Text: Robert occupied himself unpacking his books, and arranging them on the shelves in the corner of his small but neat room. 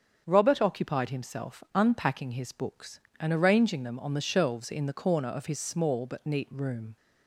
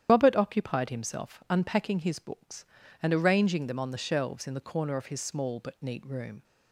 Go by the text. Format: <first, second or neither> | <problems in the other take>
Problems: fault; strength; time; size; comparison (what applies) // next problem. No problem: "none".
first | loses the start of "Robert"; at 0.0 s; 105 ms // starts louder than the rest; strong; until 1.1 s; 10 dB; also in the first